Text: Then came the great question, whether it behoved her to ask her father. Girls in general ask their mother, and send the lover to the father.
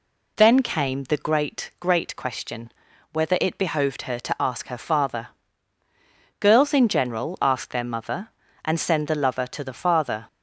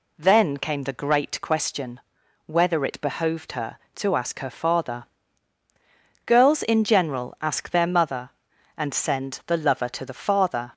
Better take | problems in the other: second | says "great" twice; at 1.7 s

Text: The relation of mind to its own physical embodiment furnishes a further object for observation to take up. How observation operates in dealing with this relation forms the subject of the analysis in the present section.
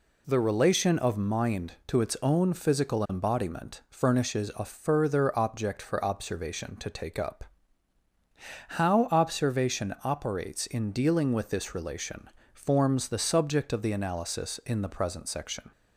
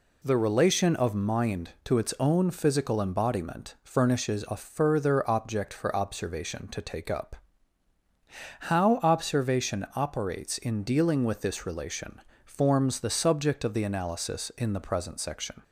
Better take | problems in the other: neither | pauses between "relation" and "forms"; slight; the same in both

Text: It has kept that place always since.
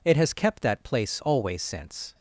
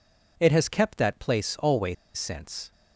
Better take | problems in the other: first | pauses between "always" and "since"; slight; at 1.9 s; 0.21 s long

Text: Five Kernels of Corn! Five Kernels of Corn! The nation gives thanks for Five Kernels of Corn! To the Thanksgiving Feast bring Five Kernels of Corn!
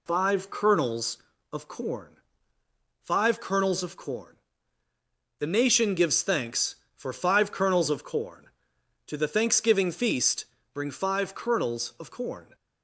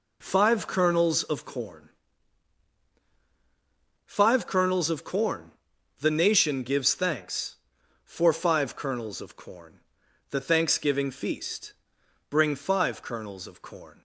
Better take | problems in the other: first | skips "To"; at 10.0 s // pauses between "Feast" and "bring"; noticeable; at 11.7 s; 0.56 s long; slight in the first

